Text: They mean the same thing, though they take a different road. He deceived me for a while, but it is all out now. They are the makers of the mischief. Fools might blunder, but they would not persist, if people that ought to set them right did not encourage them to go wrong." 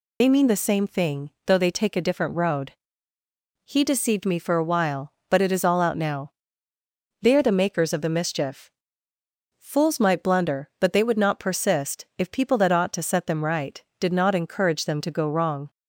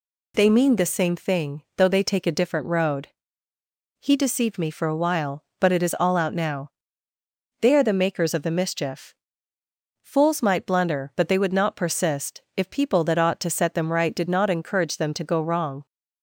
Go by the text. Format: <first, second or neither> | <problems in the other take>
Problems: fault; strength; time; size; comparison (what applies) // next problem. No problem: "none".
second | loses the start of "They"; at 0.2 s; 40 ms